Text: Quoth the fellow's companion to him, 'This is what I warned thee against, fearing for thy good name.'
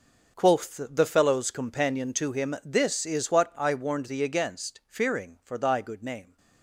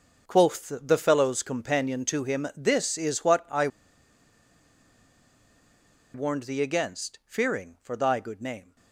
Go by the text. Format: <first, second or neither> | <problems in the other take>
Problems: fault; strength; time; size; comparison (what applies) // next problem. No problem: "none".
first | starts louder than the rest; until 1.3 s; 6.5 dB; also in the first // pauses between "I" and "warned"; strong; at 3.6 s; 2.4 s long